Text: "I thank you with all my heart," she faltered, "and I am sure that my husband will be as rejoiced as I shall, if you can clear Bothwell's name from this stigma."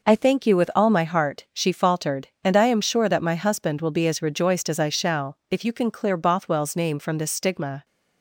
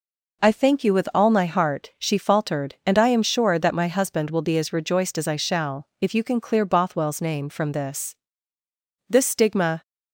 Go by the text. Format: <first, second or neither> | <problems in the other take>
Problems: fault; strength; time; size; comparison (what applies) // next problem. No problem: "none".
first | says "this" twice; at 9.0 s